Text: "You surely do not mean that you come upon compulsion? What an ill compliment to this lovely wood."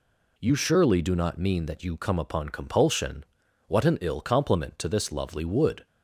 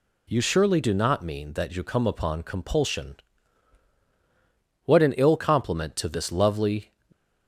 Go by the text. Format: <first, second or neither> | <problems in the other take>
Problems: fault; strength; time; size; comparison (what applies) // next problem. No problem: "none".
first | stops before "wood"; at 7.1 s